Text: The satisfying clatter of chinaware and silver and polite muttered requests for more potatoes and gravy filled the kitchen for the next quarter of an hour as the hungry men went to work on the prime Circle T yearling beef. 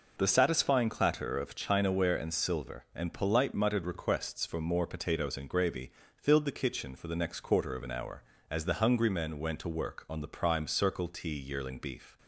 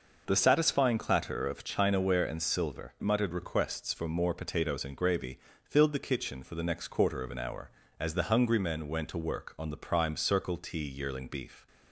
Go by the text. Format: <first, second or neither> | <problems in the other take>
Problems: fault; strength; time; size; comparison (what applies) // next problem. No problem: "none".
first | skips "and polite"; at 2.9 s // pauses between "gravy" and "filled"; slight; at 5.3 s; 0.24 s long; slight in the first